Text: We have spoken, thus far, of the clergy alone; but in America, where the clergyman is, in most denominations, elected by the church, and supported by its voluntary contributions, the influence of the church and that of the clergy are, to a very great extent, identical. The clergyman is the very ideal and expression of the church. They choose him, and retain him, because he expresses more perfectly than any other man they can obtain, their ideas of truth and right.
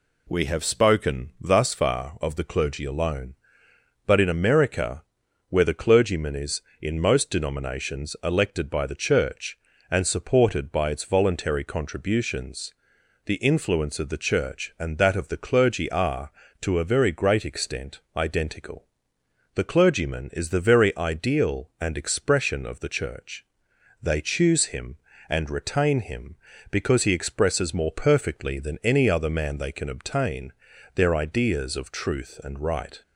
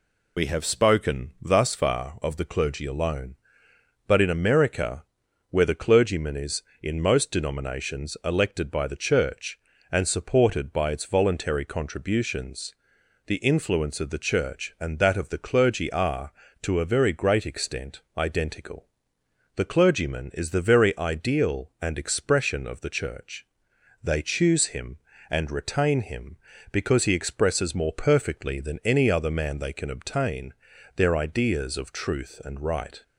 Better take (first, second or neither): first